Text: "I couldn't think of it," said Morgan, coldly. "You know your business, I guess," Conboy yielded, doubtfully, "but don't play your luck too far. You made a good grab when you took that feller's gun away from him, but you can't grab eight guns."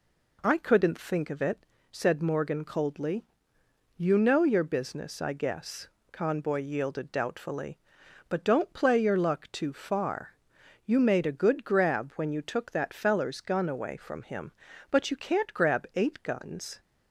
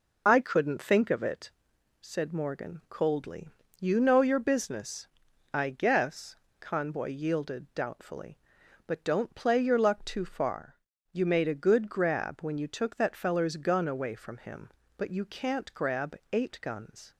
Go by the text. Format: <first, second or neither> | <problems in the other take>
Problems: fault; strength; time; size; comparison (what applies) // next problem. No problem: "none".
first | loses the start of "I"; at 0.2 s; 45 ms